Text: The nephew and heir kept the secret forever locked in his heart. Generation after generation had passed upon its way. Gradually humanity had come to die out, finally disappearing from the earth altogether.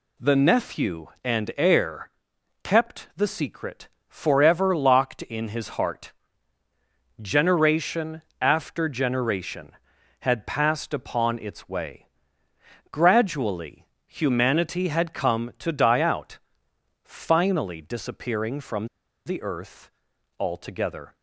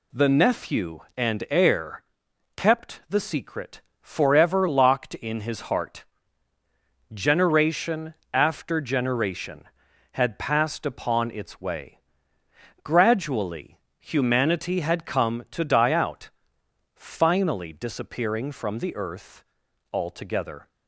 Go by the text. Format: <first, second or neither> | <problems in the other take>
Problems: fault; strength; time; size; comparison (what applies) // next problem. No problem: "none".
second | pauses between "heir" and "kept"; noticeable; at 2.0 s; 0.54 s long; noticeable in the second // pauses between "secret" and "forever"; slight; at 3.8 s; 0.18 s long; slight in the second // pauses between "Generation" and "after"; slight; at 8.2 s; 0.18 s long; slight in the second // pauses between "Gradually" and "humanity"; slight; at 13.8 s; 0.20 s long; slight in the second // pauses between "from" and "the"; at 18.8 s; 0.38 s long // pauses between "earth" and "altogether"; noticeable; at 19.8 s; 0.50 s long; noticeable in the second